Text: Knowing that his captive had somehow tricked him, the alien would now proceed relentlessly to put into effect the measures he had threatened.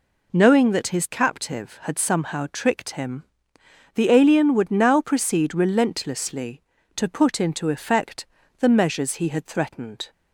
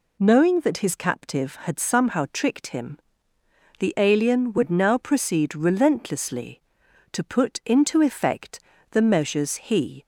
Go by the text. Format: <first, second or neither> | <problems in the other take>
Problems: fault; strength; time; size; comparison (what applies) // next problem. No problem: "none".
first | pauses between "effect" and "the"; slight; at 8.5 s; 0.32 s long; slight in the first // stops before "had threatened"; at 10.0 s